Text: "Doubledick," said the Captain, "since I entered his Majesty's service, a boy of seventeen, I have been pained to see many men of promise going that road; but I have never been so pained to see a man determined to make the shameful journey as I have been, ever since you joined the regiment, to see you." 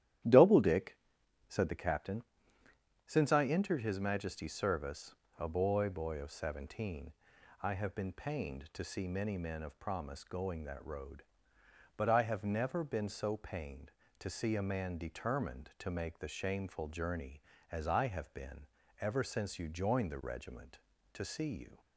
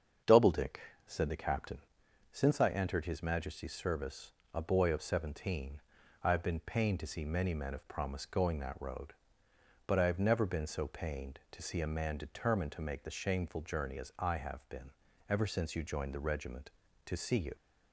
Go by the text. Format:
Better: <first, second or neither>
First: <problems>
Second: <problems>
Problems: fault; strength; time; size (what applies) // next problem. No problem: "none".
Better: second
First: starts louder than the rest; strong; until 1.7 s; 12 dB // says "boy" twice; at 5.8 s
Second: starts louder than the rest; strong; until 1.5 s; 7 dB